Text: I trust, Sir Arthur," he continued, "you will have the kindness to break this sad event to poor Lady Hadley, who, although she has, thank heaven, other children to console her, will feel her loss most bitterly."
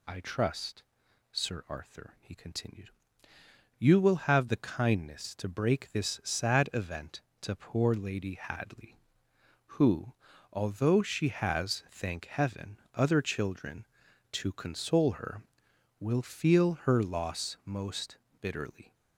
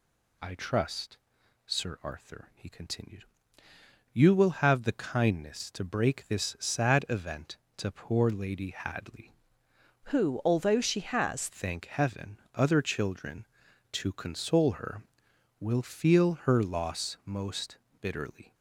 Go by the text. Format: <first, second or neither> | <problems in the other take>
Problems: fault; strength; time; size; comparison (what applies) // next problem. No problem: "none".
first | changes voice from "who" to "has"; from 10.0 to 11.4 s; 1.4 s long // pauses between "most" and "bitterly"; slight; at 17.7 s; 0.24 s long; slight in the first